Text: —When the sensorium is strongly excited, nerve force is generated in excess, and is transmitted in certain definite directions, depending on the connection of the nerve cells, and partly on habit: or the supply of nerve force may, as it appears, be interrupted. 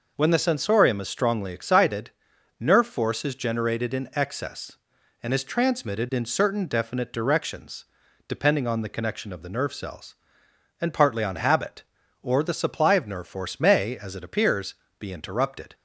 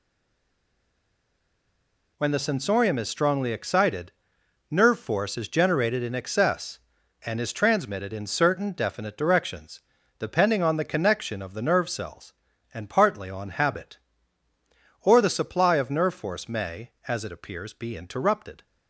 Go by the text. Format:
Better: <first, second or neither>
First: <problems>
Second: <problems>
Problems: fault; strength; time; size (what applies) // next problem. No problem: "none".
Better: first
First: none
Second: stays silent before the first word; until 2.1 s; 2.1 s long